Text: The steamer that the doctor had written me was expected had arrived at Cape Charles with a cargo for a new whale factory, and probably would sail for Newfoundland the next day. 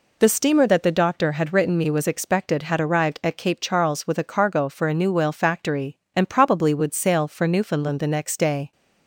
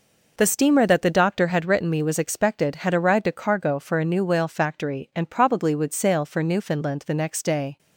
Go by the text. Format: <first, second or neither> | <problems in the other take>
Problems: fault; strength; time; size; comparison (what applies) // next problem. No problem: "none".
first | skips "at Cape Charles with"; at 3.2 s